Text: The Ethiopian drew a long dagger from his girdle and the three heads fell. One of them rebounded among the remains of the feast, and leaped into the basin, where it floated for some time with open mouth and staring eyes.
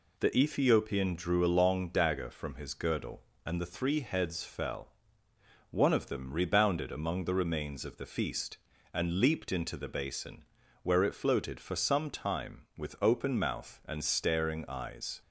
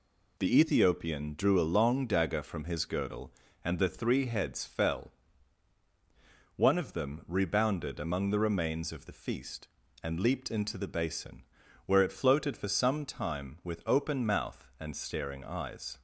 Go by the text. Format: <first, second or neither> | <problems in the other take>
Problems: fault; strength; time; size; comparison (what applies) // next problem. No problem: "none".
neither | none